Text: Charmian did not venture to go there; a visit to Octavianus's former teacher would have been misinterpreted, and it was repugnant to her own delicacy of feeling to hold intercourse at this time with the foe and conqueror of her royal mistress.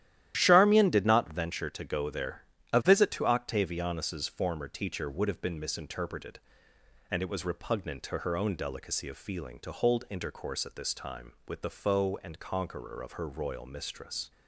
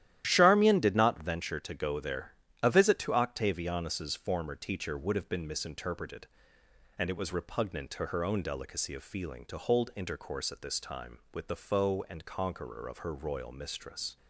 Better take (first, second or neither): neither